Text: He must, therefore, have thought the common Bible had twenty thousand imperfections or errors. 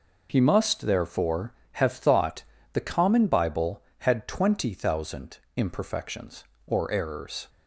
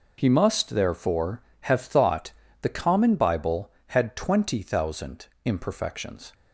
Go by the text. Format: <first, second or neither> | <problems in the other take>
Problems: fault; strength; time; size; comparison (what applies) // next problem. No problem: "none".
first | pauses between "thought" and "the"; slight; at 2.3 s; 0.28 s long; slight in the first // pauses between "thousand" and "imperfections"; slight; at 5.2 s; 0.18 s long; slight in the first // stops before "or errors"; at 6.3 s